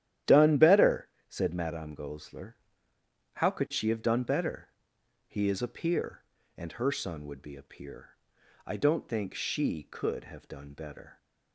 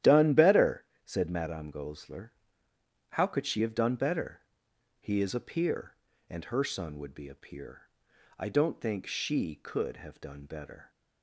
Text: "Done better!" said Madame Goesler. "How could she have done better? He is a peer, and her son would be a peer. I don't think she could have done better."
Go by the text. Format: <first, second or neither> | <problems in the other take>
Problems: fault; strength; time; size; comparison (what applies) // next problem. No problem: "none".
neither | starts louder than the rest; strong; the same in both